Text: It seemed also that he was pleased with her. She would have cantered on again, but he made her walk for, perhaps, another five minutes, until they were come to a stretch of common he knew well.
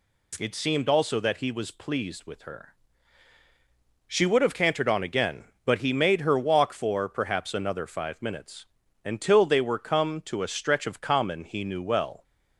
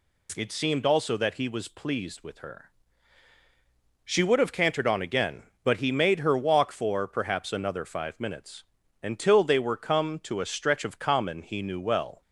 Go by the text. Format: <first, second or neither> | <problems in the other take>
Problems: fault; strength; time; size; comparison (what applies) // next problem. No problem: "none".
neither | none